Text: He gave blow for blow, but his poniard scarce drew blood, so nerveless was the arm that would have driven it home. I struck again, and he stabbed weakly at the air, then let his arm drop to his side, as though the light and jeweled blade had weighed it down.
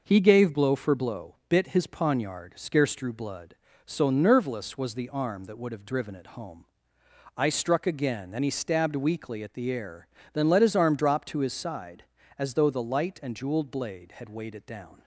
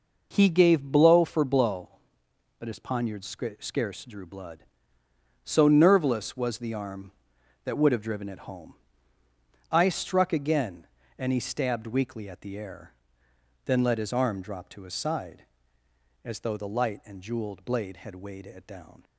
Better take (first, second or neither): second